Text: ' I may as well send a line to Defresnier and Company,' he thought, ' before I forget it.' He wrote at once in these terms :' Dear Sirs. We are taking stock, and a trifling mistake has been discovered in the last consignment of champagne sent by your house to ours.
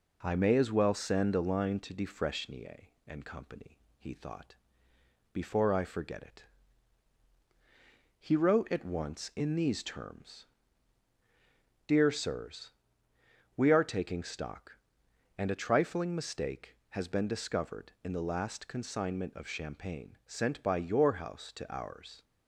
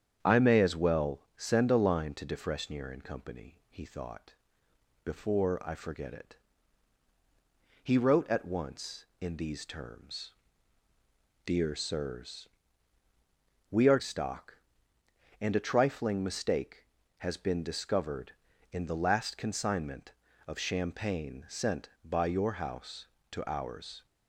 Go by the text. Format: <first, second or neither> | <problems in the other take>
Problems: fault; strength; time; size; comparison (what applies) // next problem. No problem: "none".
first | starts louder than the rest; strong; until 1.2 s; 9 dB // skips "taking"; at 13.9 s